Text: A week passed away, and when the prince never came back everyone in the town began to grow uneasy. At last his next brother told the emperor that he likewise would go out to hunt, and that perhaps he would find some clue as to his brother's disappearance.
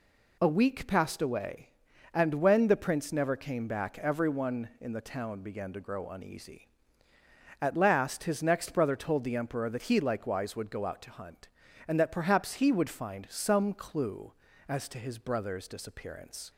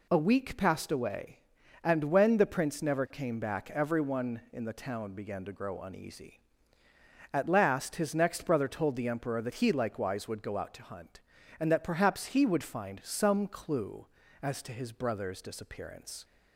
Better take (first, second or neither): neither